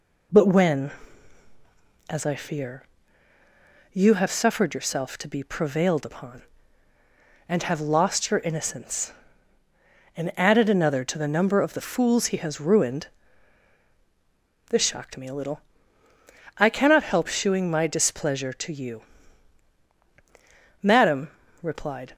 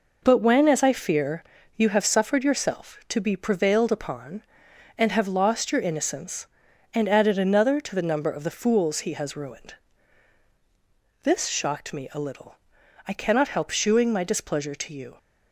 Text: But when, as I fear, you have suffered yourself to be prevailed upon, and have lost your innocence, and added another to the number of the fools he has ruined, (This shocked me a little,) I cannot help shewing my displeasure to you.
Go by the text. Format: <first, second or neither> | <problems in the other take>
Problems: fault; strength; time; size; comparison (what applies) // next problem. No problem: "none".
second | goes on to say "Madam replied"; from 20.8 s on; 1.3 s long